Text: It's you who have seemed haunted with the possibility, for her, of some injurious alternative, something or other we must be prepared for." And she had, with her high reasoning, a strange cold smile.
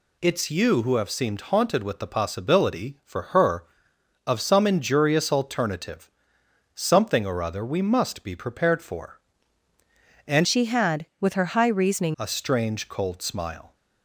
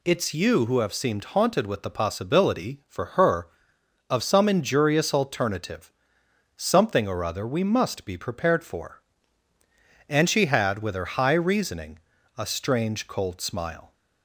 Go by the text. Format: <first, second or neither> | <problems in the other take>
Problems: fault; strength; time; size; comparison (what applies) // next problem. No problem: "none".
second | changes voice from "she" to "reasoning"; from 10.4 to 12.1 s; 1.7 s long